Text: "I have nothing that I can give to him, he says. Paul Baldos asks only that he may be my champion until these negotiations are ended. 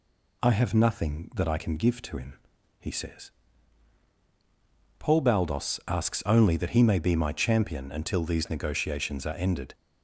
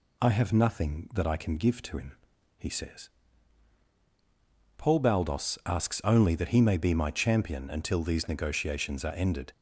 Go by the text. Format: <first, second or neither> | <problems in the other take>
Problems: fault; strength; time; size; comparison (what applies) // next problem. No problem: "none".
neither | none